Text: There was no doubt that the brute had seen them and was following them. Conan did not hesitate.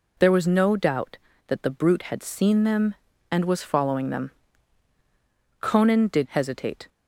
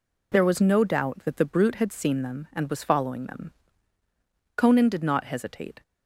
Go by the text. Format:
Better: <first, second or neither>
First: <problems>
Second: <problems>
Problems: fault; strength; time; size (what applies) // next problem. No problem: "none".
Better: second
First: skips "not"; at 6.2 s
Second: none